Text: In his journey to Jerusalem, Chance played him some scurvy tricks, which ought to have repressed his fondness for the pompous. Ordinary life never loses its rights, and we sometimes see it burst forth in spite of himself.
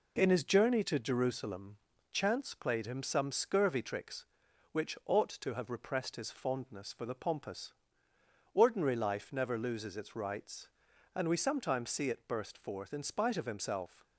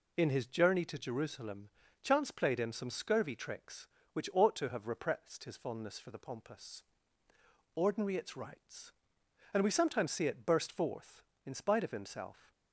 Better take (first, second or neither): first